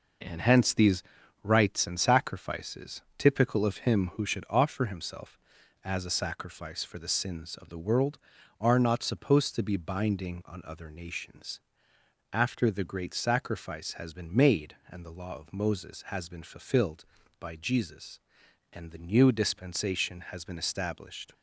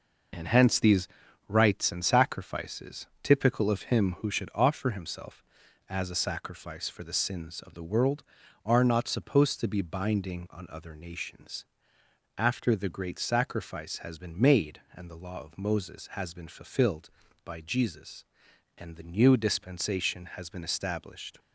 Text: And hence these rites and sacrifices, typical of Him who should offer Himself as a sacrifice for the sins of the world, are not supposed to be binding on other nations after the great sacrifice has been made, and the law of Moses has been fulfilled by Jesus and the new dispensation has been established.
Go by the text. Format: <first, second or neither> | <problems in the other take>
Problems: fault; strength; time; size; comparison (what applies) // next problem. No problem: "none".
first | loses the start of "And"; at 0.3 s; 60 ms // pauses between "these" and "rites"; at 1.0 s; 0.42 s long; also in the first // pauses between "nations" and "after"; noticeable; at 11.6 s; 0.74 s long; noticeable in the first